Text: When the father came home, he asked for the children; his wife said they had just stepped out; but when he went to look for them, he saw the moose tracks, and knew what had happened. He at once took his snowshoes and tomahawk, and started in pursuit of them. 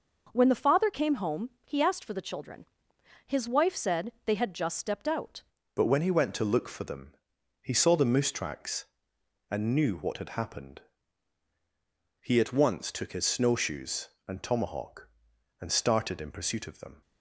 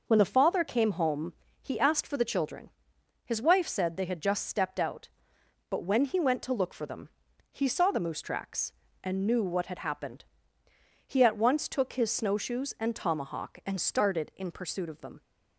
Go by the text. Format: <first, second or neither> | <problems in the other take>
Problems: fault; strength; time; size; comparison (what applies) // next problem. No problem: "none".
second | changes voice at "but"; from 5.7 s on; 11.3 s long